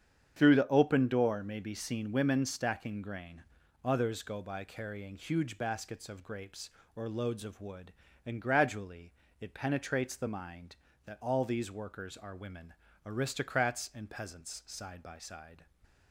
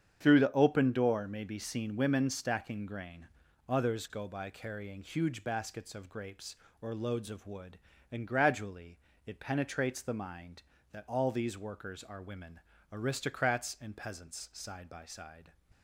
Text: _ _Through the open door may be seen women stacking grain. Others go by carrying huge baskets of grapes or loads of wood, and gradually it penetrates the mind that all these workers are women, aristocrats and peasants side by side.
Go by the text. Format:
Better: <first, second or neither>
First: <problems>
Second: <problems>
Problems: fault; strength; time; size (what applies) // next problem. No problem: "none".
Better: neither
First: starts louder than the rest; strong; until 1.3 s; 8 dB // pauses between "gradually" and "it"; slight; at 9.1 s; 0.26 s long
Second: starts louder than the rest; strong; until 1.2 s; 8 dB // pauses between "gradually" and "it"; slight; at 8.9 s; 0.26 s long